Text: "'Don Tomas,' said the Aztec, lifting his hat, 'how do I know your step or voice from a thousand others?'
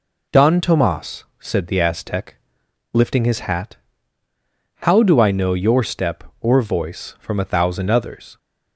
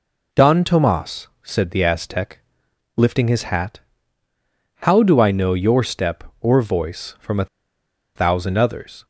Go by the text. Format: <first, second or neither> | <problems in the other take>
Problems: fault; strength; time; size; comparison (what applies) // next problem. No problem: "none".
first | pauses between "a" and "thousand"; noticeable; at 7.4 s; 0.70 s long